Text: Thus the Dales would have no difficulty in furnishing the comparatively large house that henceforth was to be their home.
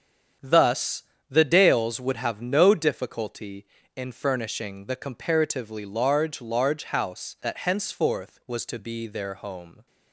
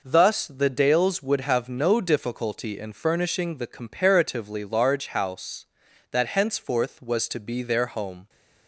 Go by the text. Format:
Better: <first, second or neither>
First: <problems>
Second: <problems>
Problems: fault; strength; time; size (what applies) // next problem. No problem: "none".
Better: second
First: starts louder than the rest; strong; until 1.6 s; 8 dB // pauses between "Thus" and "the"; slight; at 1.0 s; 0.26 s long // says "large" twice; at 6.4 s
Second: none